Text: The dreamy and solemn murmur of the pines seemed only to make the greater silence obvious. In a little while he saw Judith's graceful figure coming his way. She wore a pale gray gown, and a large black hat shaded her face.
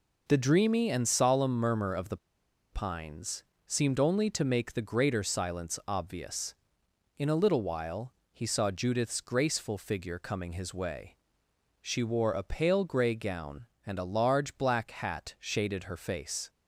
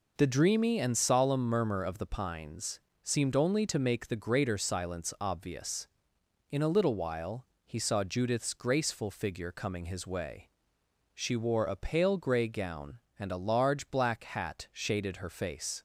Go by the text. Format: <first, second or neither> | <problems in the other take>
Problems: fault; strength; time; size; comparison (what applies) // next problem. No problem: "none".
second | pauses between "the" and "pines"; noticeable; at 2.1 s; 0.55 s long // pauses between "pines" and "seemed"; slight; at 3.4 s; 0.24 s long; slight in the second // pauses between "while" and "he"; slight; at 8.1 s; 0.18 s long; slight in the second